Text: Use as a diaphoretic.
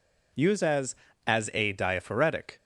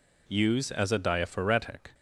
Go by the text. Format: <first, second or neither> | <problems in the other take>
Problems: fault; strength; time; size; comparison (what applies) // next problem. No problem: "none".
second | says "as" twice; at 1.2 s